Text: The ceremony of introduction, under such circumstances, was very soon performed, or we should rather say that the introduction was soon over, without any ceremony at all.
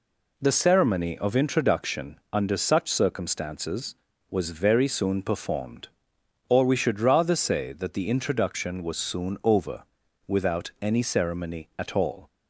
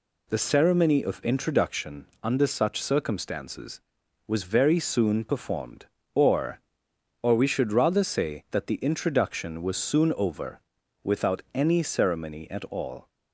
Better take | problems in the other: first | says "or" twice; at 7.2 s

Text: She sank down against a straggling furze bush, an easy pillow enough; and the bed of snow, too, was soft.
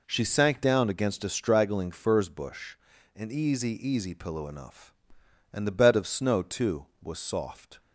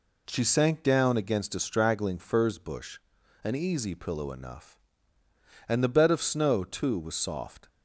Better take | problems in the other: second | says "easy" twice; at 3.8 s

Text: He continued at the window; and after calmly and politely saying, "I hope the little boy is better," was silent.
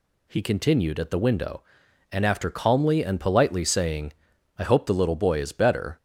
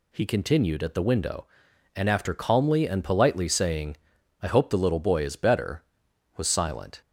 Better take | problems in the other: second | stops before "was silent"; at 5.9 s

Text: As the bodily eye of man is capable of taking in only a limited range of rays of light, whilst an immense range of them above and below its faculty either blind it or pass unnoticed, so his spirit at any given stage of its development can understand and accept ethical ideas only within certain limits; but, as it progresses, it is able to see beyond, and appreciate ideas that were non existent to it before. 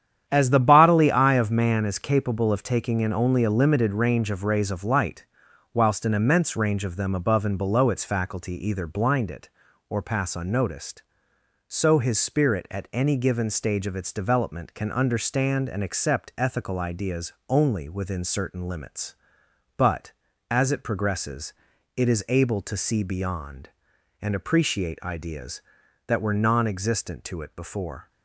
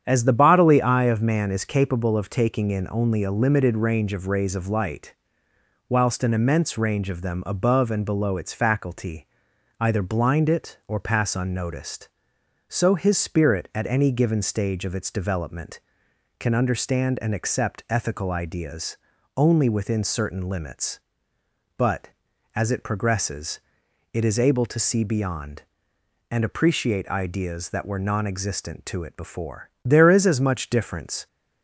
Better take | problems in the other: first | starts louder than the rest; strong; until 1.0 s; 8.5 dB; strong in the first // pauses between "faculty" and "either"; noticeable; at 9.2 s; 0.54 s long // pauses between "ideas" and "only"; at 18.9 s; 0.38 s long; slight in the first // goes on to say "There is as much difference"; from 29.8 s on; 1.4 s long

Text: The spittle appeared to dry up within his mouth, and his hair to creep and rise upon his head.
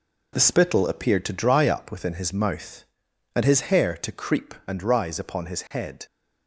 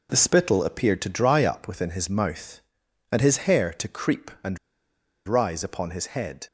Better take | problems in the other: first | pauses between "and" and "rise"; noticeable; at 4.5 s; 0.68 s long

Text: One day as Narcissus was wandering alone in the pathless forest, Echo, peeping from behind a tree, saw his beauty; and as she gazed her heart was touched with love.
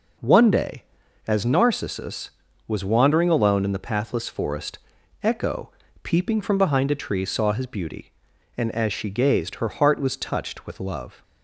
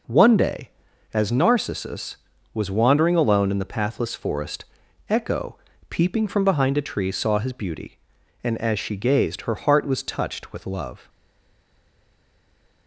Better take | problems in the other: first | stays silent after the last word; noticeable; from 11.0 s on; 1.8 s long

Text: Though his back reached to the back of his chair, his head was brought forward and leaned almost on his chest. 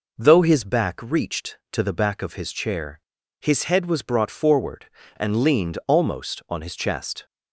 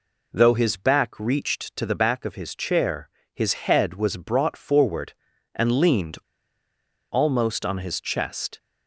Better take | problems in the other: first | pauses between "leaned" and "almost"; noticeable; at 6.1 s; 0.94 s long

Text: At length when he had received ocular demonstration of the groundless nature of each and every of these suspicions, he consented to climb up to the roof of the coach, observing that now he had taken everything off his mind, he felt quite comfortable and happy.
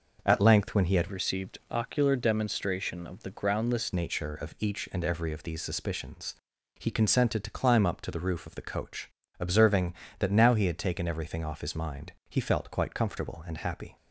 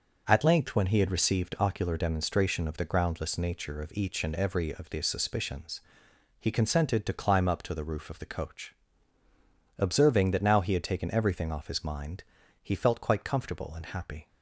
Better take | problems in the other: second | changes voice from "received" to "groundless"; from 1.0 to 3.9 s; 2.9 s long

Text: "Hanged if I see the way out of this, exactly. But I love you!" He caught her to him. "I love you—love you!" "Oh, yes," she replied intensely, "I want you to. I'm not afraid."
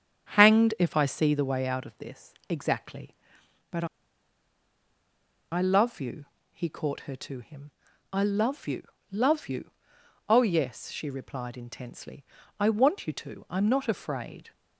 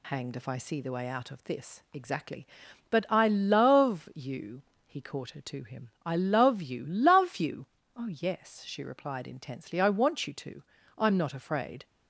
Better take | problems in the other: second | starts louder than the rest; strong; until 1.3 s; 8 dB // pauses between "But" and "I"; strong; at 3.8 s; 1.6 s long

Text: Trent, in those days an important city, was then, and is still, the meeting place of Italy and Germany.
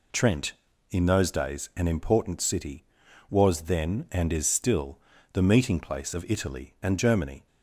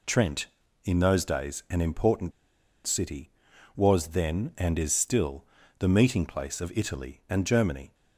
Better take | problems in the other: first | pauses between "important" and "city"; noticeable; at 2.3 s; 0.54 s long

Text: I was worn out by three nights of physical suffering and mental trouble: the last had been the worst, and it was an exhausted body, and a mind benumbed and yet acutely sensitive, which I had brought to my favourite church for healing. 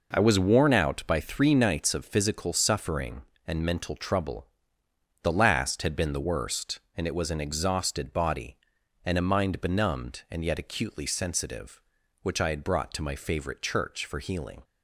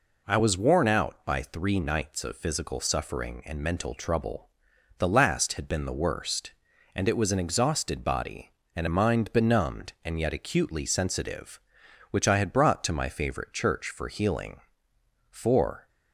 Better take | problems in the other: first | goes on to say "For"; from 15.3 s on; 0.56 s long

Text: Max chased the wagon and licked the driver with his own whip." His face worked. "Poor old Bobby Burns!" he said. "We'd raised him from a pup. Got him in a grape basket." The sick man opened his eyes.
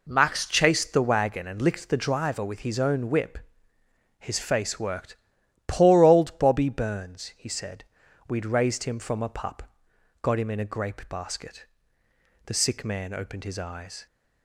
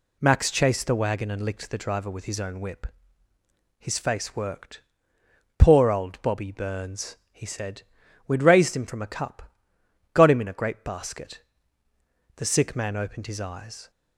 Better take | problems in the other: first | says "cup" for "pup"; at 9.0 s

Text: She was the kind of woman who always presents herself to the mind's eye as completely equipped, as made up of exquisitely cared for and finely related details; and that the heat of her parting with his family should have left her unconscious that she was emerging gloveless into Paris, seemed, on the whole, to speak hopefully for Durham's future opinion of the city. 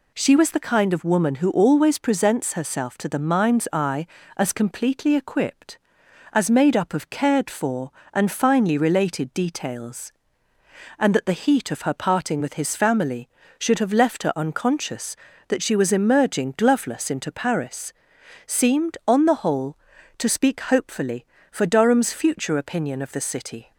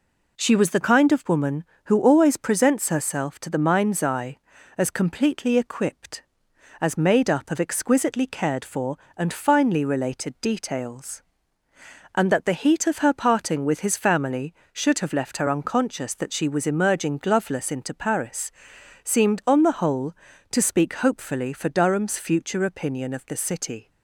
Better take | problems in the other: second | skips "exquisitely"; at 7.0 s

